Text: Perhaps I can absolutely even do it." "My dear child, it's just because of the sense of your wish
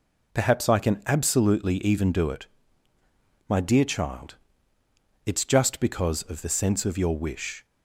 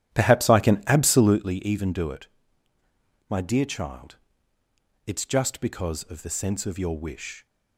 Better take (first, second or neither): first